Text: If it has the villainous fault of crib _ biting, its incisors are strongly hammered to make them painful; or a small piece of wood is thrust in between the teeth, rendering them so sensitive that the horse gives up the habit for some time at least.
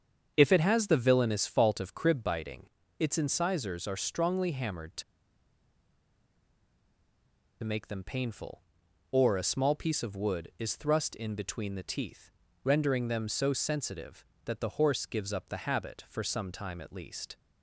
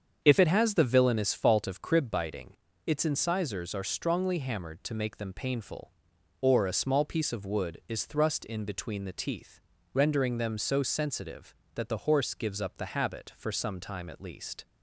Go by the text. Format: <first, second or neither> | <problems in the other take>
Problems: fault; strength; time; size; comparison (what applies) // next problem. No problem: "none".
second | starts louder than the rest; strong; until 1.3 s; 7.5 dB; strong in the second // pauses between "to" and "make"; strong; at 5.0 s; 2.6 s long